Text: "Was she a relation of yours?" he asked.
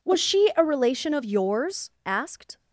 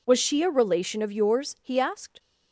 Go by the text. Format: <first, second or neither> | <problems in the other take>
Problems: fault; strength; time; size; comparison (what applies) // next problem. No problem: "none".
second | skips "he"; at 1.9 s